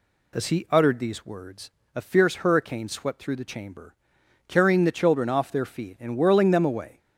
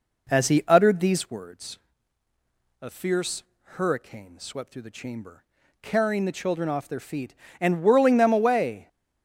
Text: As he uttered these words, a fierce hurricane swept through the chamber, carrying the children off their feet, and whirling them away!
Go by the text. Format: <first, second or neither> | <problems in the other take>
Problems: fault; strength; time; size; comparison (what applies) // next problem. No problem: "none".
first | starts louder than the rest; noticeable; until 1.4 s; 4 dB // pauses between "fierce" and "hurricane"; slight; at 3.4 s; 0.18 s long